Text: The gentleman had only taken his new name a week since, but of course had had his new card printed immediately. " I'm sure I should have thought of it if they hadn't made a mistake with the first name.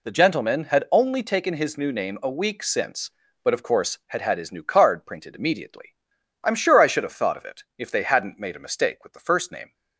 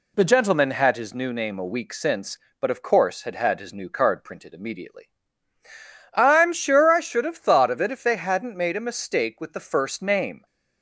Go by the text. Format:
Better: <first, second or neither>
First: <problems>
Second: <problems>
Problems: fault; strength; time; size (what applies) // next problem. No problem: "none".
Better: first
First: none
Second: skips "only taken"; at 0.9 s